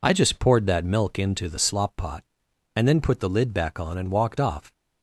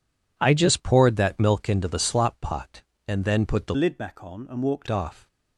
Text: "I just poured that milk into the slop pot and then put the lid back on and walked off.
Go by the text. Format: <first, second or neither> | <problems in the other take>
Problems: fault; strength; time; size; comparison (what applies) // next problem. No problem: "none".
first | changes voice from "lid" to "walked"; from 3.7 to 4.8 s; 1.1 s long